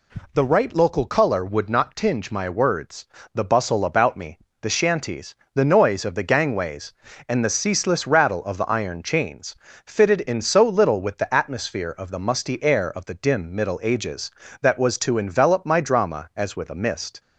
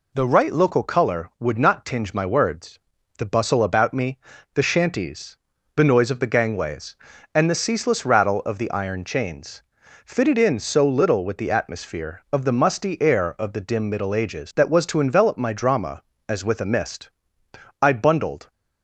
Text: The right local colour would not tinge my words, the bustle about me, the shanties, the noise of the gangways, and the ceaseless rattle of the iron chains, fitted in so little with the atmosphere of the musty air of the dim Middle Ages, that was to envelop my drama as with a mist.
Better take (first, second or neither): first